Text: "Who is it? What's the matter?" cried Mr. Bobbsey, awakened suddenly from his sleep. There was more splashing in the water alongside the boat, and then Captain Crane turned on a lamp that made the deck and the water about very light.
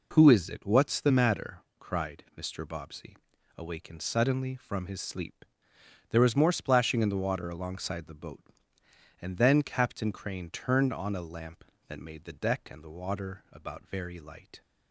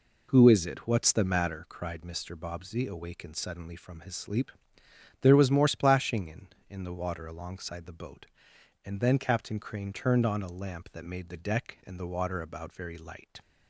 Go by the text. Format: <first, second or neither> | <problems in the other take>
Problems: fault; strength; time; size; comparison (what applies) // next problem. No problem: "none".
first | says "in" twice; at 6.6 s